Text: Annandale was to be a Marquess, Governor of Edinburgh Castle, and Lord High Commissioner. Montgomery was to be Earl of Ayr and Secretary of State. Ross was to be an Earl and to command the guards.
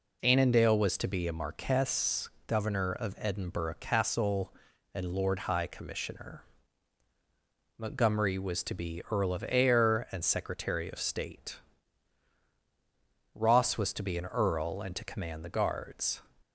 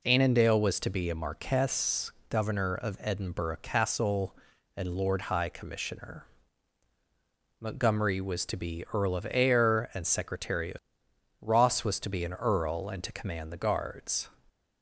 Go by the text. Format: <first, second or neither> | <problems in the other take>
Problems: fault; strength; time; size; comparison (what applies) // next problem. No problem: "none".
first | skips "State"; at 11.0 s